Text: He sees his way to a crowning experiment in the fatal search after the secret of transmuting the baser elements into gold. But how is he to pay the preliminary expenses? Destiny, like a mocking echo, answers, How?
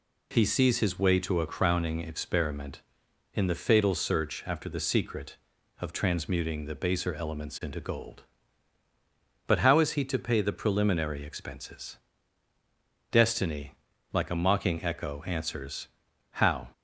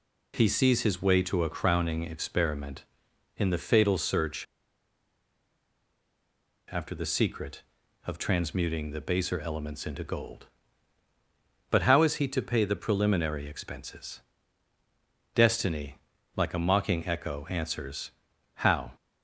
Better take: first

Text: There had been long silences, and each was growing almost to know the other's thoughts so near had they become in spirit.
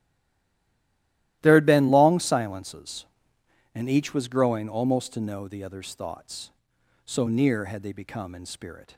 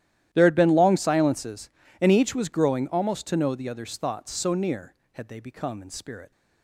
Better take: second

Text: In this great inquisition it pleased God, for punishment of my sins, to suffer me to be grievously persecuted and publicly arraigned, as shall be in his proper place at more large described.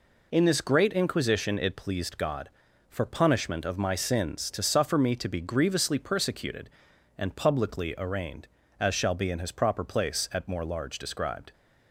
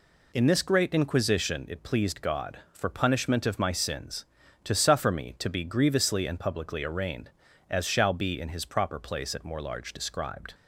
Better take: first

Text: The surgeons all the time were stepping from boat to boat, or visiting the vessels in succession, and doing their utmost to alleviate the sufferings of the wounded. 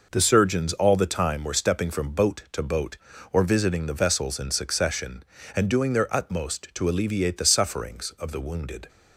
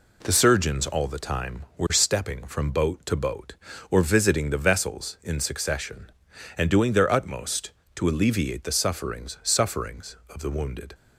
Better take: first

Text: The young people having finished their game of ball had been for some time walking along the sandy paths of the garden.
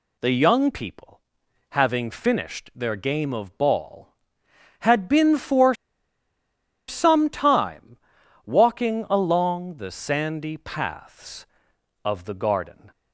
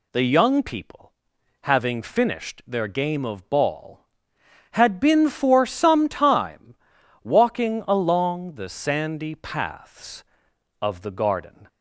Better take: second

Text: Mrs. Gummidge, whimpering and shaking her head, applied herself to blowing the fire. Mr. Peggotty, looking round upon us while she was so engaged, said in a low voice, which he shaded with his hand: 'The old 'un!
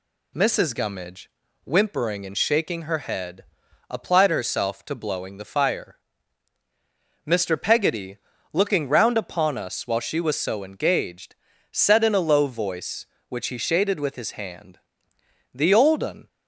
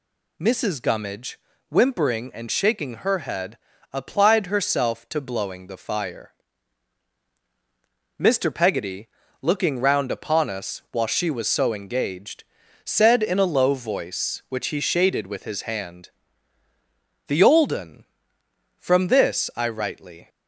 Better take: first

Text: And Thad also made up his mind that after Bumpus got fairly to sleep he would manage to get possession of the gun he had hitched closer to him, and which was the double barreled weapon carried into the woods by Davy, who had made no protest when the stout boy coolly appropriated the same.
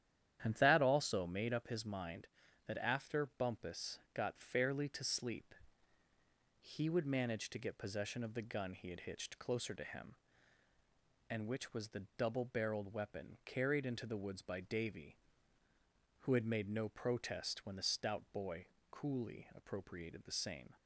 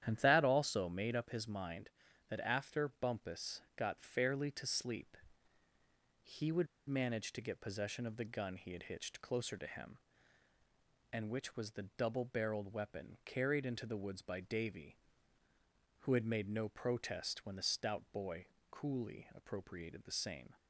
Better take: first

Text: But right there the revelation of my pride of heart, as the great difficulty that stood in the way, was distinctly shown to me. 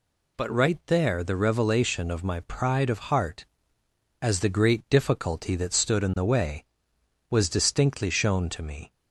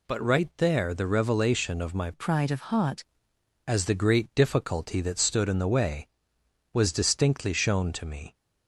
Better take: first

